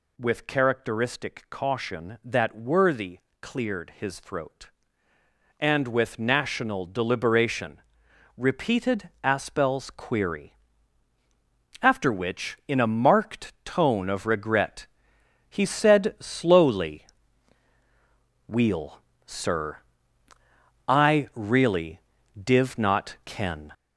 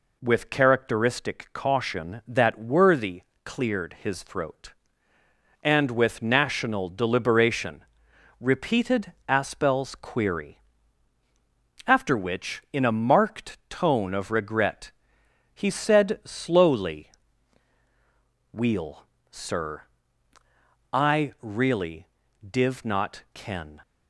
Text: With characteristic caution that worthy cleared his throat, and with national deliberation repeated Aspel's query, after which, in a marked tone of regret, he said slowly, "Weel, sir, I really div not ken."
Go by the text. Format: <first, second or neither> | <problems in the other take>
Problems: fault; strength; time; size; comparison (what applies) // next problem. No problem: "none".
second | gets louder; noticeable; throughout; 5 dB // pauses between "worthy" and "cleared"; slight; at 3.1 s; 0.24 s long; slight in the second // pauses between "deliberation" and "repeated"; noticeable; at 7.8 s; 0.56 s long; noticeable in the second // pauses between "really" and "div"; at 21.9 s; 0.40 s long; also in the second